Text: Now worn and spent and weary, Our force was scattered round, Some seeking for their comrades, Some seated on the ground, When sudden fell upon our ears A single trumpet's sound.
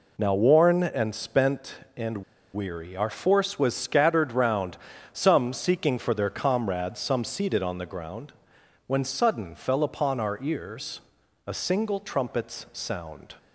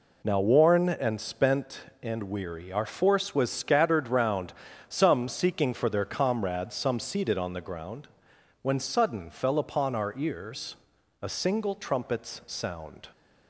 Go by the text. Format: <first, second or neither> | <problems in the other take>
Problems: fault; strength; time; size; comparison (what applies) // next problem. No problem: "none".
second | pauses between "and" and "weary"; slight; at 2.1 s; 0.36 s long // pauses between "ears" and "A"; at 11.0 s; 0.44 s long; also in the second